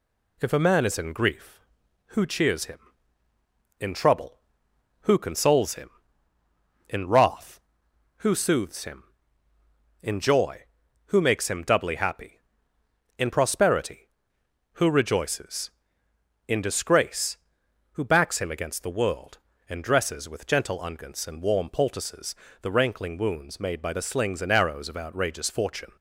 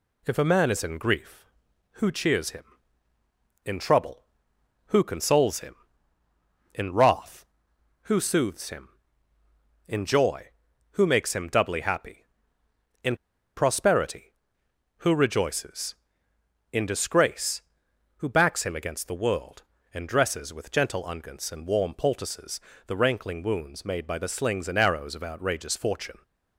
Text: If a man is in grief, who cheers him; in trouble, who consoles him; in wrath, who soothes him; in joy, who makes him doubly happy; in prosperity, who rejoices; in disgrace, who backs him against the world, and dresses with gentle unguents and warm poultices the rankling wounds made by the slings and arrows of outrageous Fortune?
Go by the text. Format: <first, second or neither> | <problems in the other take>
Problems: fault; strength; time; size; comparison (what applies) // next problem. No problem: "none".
first | pauses between "in" and "prosperity"; at 13.1 s; 0.39 s long // pauses between "poultices" and "the"; slight; at 22.6 s; 0.26 s long; slight in the first